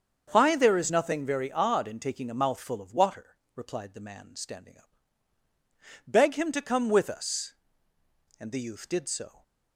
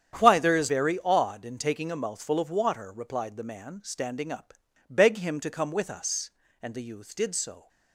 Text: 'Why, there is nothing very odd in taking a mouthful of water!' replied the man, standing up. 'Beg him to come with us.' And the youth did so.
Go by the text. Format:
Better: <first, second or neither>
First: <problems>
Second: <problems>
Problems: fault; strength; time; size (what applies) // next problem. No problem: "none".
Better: first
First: starts louder than the rest; until 1.3 s; 7 dB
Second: starts louder than the rest; strong; until 1.2 s; 9 dB // skips "nothing"; at 0.6 s